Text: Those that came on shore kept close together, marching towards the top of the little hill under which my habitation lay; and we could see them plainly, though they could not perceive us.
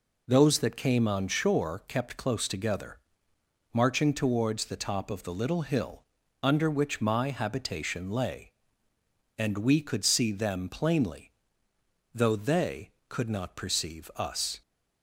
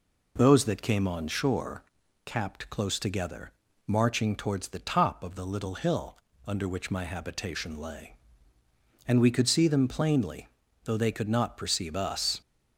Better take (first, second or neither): first